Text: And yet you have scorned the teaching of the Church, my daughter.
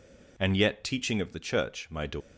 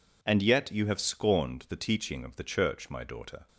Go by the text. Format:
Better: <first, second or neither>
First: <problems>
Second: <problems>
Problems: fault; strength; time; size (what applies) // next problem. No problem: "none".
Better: second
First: skips "you have scorned the"; at 0.8 s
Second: none